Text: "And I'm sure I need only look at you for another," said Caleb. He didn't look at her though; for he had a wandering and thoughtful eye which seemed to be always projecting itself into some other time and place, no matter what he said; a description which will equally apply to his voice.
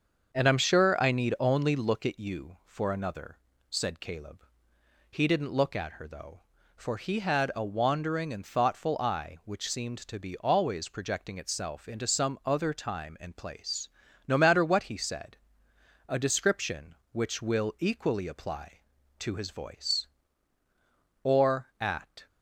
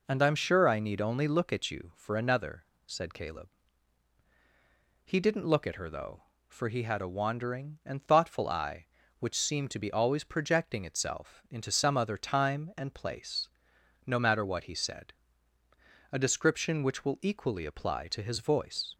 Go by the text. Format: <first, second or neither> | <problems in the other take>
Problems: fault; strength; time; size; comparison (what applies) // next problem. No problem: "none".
second | starts louder than the rest; until 1.4 s; 6.5 dB // goes on to say "Or at"; noticeable; from 21.2 s on; 1.0 s long